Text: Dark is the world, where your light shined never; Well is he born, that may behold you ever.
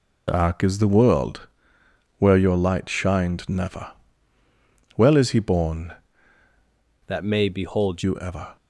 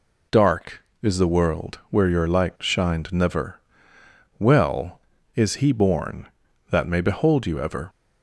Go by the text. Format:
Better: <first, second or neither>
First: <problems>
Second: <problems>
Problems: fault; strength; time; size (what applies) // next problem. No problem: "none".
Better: second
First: changes voice from "that" to "behold"; from 7.0 to 8.0 s; 1.0 s long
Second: none